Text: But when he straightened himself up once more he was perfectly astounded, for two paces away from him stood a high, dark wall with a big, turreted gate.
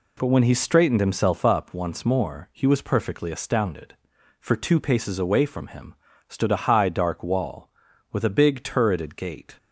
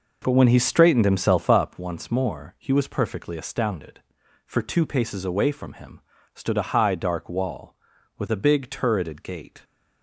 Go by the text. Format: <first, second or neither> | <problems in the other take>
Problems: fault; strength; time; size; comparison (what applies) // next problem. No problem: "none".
first | starts louder than the rest; noticeable; until 1.8 s; 5.5 dB // pauses between "him" and "stood"; slight; at 5.9 s; 0.34 s long; slight in the first